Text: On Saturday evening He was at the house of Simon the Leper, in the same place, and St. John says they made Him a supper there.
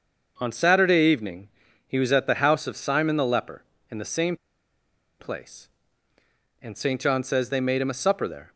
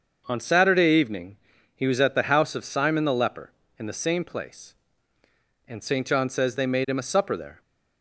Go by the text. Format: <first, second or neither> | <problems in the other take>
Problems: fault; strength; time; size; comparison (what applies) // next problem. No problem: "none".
second | starts louder than the rest; until 1.3 s; 6.5 dB; also in the second // pauses between "evening" and "He"; at 1.4 s; 0.38 s long; also in the second // pauses between "same" and "place"; noticeable; at 4.3 s; 0.85 s long